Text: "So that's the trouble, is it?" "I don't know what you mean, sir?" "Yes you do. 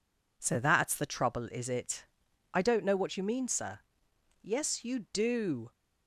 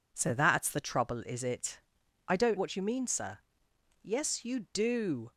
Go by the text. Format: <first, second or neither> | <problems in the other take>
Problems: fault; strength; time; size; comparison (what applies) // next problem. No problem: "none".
first | skips "know"; at 2.5 s